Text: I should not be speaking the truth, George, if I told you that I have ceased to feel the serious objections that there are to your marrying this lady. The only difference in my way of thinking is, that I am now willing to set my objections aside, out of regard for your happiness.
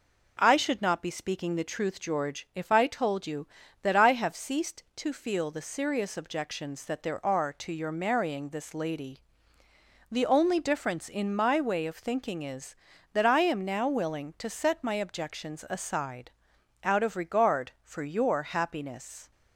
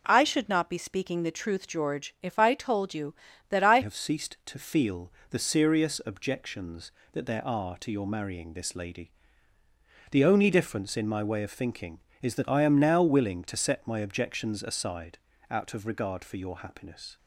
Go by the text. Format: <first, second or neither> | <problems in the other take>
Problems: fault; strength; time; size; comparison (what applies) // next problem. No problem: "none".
first | changes voice at "have"; from 3.8 s on; 13.3 s long // pauses between "feel" and "the"; slight; at 5.1 s; 0.18 s long